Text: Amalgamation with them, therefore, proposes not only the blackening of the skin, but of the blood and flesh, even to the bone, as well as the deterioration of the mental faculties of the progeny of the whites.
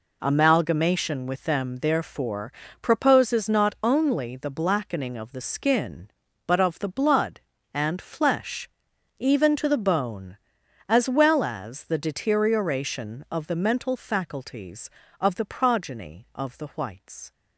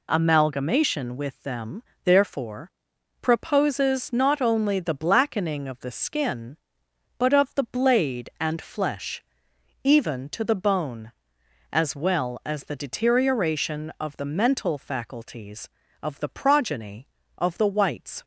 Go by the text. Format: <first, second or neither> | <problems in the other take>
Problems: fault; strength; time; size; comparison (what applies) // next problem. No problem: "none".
first | says "blade" for "blood"; at 7.6 s